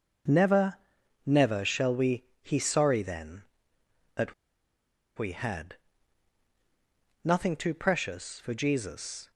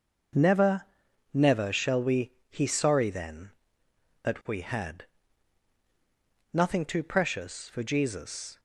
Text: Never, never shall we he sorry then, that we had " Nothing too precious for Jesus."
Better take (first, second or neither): second